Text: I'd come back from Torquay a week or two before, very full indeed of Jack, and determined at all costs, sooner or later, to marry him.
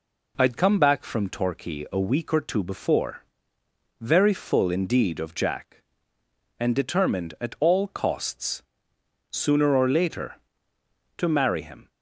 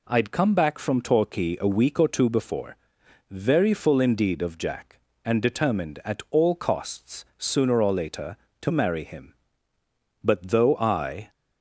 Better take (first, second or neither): first